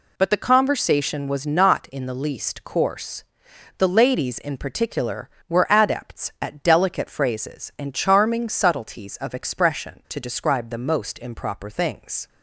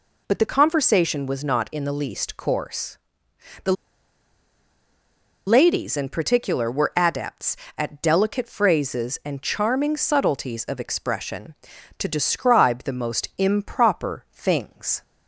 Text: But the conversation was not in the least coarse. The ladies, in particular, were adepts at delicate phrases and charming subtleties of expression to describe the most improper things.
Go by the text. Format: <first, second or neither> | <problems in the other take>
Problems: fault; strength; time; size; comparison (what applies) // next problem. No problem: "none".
first | pauses between "The" and "ladies"; strong; at 3.7 s; 1.7 s long